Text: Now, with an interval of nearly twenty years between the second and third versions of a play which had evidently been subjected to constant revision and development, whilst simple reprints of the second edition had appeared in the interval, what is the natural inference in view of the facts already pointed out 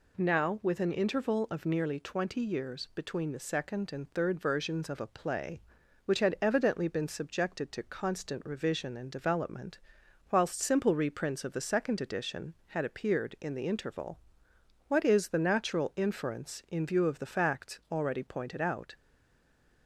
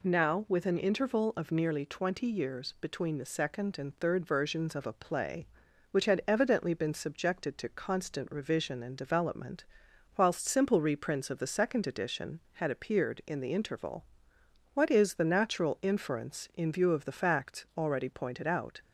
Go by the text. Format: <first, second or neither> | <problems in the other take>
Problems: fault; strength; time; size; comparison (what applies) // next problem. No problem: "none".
second | stays silent after the last word; slight; from 18.9 s on; 0.9 s long